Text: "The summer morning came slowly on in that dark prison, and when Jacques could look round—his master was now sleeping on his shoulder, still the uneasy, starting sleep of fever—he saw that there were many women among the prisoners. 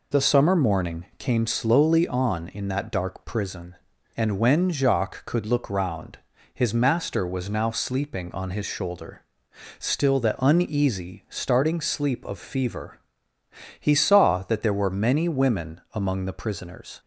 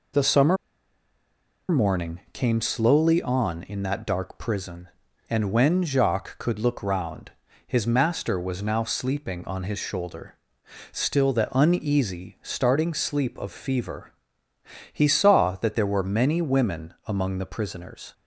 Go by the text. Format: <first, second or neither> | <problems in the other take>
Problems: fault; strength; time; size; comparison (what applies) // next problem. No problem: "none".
first | pauses between "summer" and "morning"; at 0.5 s; 1.1 s long